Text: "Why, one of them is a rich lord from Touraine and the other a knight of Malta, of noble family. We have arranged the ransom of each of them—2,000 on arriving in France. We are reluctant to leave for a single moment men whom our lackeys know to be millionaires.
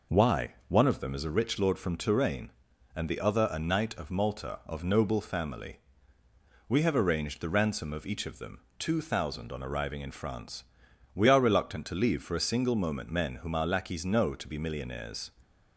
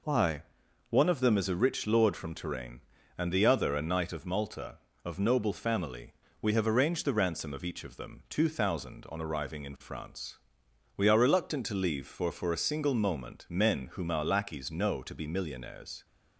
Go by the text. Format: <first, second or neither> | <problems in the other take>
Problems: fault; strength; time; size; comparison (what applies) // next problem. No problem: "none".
first | says "for" twice; at 12.3 s